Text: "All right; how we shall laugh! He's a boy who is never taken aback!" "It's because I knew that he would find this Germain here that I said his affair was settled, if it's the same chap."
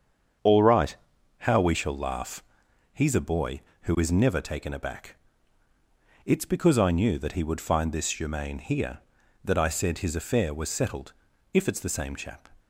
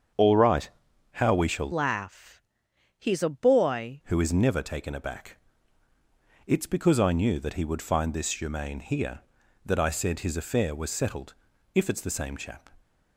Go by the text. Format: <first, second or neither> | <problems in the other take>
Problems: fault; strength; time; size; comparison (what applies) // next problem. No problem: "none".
first | starts louder than the rest; strong; until 1.5 s; 7 dB; strong in the first // changes voice from "laugh" to "boy"; from 1.7 to 4.0 s; 2.3 s long